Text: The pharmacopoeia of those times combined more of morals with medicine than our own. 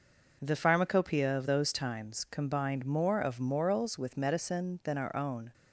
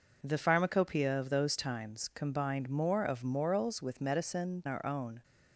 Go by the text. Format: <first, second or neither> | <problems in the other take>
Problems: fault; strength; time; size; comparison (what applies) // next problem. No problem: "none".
first | skips "than"; at 4.6 s